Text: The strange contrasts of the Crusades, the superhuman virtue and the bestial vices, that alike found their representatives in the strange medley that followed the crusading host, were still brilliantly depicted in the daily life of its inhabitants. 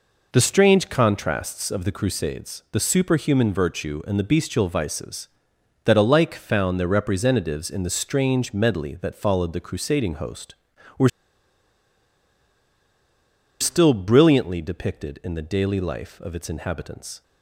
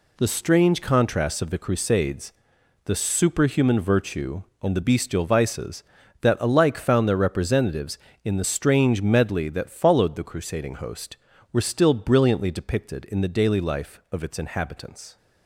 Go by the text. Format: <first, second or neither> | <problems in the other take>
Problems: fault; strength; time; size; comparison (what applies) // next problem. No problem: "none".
second | pauses between "were" and "still"; strong; at 11.0 s; 2.5 s long